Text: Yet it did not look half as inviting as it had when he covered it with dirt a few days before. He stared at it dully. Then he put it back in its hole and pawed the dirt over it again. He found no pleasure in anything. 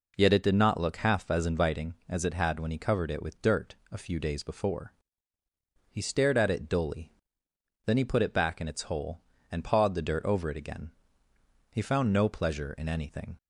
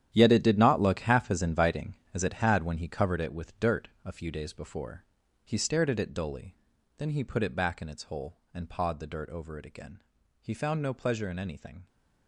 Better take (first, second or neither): first